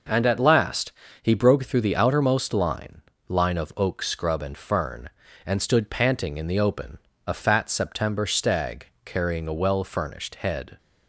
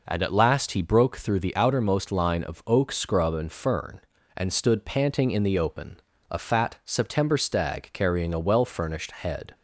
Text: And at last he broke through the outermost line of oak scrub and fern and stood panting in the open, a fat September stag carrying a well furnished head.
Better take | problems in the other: second | pauses between "last" and "he"; slight; at 0.9 s; 0.30 s long // says "line" twice; at 3.2 s // pauses between "stag" and "carrying"; slight; at 8.8 s; 0.16 s long

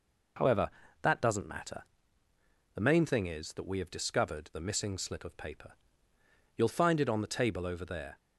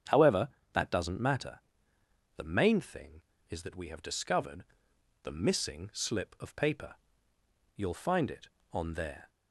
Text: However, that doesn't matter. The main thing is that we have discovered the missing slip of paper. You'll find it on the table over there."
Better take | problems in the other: first | starts louder than the rest; strong; until 1.3 s; 8.5 dB // pauses between "discovered" and "the"; noticeable; at 4.6 s; 0.60 s long // skips "the table over"; at 8.9 s

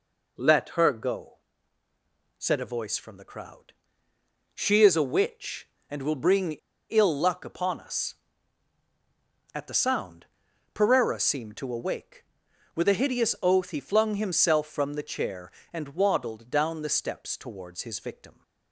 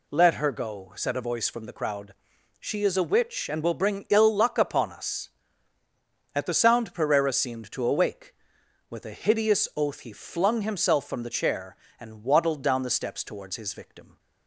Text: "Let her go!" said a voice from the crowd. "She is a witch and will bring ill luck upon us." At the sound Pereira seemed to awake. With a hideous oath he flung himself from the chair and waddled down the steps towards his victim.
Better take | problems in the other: second | pauses between "bring" and "ill"; at 6.5 s; 0.38 s long // pauses between "sound" and "Pereira"; noticeable; at 10.2 s; 0.48 s long

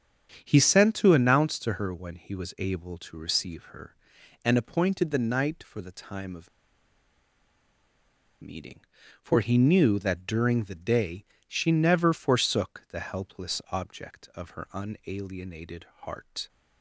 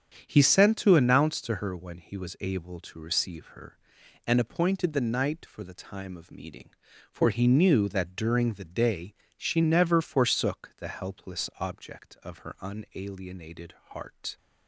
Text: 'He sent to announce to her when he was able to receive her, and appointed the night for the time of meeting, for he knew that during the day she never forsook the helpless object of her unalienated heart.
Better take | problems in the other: second | starts louder than the rest; strong; until 1.4 s; 8 dB; strong in the second // pauses between "of" and "meeting"; strong; at 6.4 s; 1.9 s long // pauses between "day" and "she"; slight; at 11.2 s; 0.24 s long; slight in the second // pauses between "unalienated" and "heart"; slight; at 15.8 s; 0.18 s long; slight in the second

